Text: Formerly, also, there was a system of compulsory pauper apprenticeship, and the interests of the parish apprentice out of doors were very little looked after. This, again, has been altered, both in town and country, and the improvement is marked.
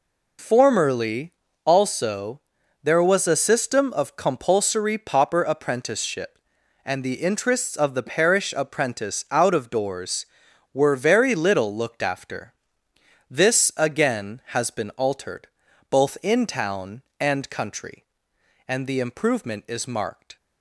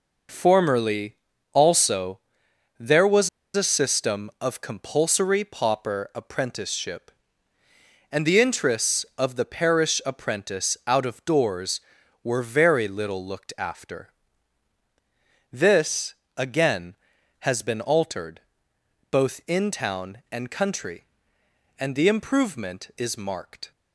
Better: first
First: none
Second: pauses between "was" and "a"; slight; at 3.2 s; 0.28 s long

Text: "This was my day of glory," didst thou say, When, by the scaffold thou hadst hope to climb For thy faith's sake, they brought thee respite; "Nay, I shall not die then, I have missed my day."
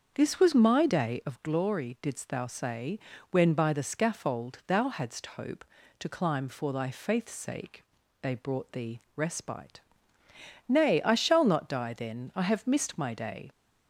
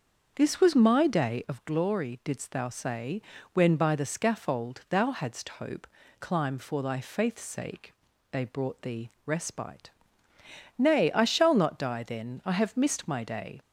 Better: first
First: starts louder than the rest; until 1.1 s; 7 dB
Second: starts louder than the rest; until 1.3 s; 7 dB // skips "to"; at 6.0 s

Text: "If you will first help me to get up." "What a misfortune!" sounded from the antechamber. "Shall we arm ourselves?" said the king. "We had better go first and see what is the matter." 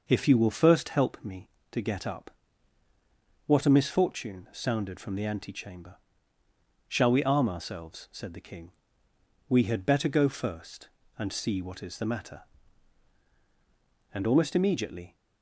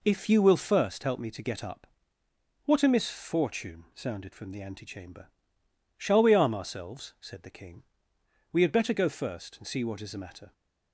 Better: second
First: goes on to say "And almost immediately"; noticeable; from 14.1 s on; 1.0 s long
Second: none

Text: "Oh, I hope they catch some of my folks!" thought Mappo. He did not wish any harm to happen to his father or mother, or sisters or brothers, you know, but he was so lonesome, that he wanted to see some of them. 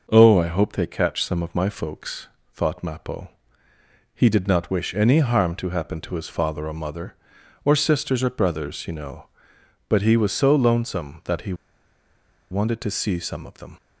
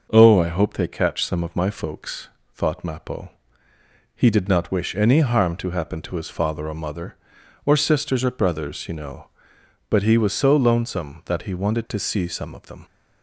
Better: second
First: pauses between "he" and "wanted"; noticeable; at 11.5 s; 0.97 s long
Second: none

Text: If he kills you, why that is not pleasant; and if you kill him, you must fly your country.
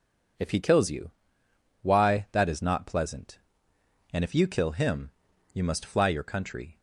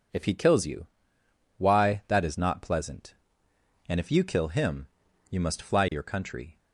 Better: neither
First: none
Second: none

